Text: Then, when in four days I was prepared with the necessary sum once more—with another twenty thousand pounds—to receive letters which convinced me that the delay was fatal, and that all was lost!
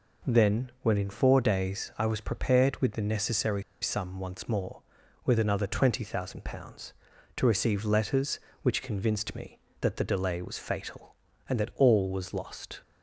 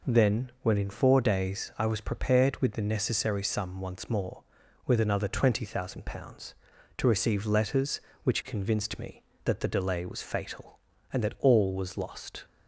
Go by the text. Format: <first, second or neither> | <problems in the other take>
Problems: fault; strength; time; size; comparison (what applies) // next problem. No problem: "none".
second | pauses between "necessary" and "sum"; slight; at 3.6 s; 0.20 s long